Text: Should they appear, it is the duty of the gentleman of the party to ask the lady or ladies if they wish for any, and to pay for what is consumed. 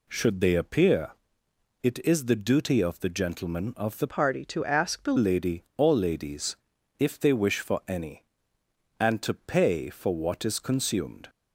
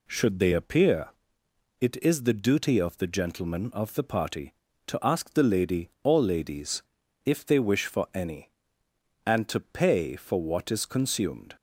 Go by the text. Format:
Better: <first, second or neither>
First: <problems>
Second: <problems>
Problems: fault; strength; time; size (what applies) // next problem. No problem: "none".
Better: second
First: changes voice from "party" to "the"; from 4.0 to 5.1 s; 1.1 s long // pauses between "ladies" and "if"; at 6.5 s; 0.42 s long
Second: pauses between "ladies" and "if"; at 6.8 s; 0.42 s long